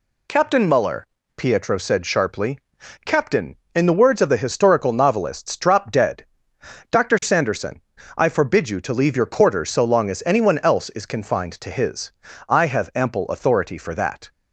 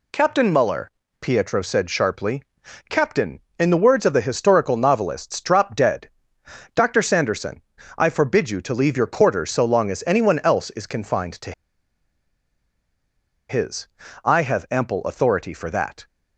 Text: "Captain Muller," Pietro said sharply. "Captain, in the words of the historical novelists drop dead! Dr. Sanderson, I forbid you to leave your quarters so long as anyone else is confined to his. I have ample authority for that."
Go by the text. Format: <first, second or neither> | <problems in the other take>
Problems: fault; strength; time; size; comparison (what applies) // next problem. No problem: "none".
first | pauses between "to" and "his"; strong; at 11.5 s; 1.9 s long